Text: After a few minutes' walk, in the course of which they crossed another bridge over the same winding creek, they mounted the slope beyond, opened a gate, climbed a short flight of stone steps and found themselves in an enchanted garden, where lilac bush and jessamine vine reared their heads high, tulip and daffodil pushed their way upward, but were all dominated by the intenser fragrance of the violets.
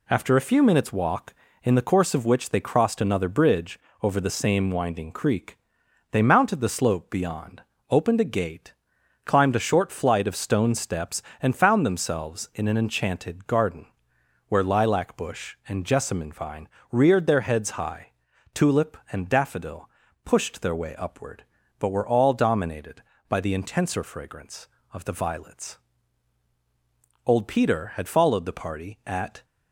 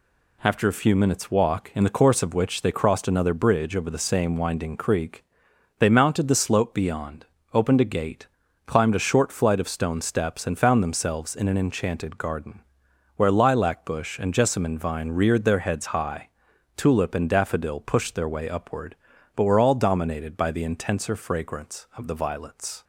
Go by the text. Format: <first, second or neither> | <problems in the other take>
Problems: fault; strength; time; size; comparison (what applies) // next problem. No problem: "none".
second | pauses between "bridge" and "over"; slight; at 3.7 s; 0.24 s long // pauses between "vine" and "reared"; slight; at 16.6 s; 0.22 s long // pauses between "daffodil" and "pushed"; slight; at 19.8 s; 0.34 s long // goes on to say "Old Peter had followed the party at"; strong; from 27.2 s on; 2.2 s long